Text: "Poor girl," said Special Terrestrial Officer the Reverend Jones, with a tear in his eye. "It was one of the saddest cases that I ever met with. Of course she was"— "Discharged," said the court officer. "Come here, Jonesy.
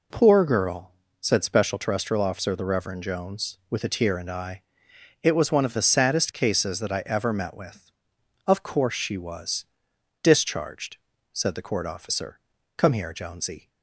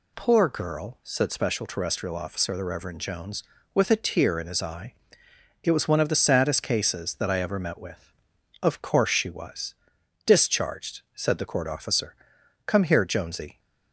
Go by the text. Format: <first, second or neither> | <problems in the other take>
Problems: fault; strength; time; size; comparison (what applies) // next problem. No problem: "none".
second | skips "his"; at 4.2 s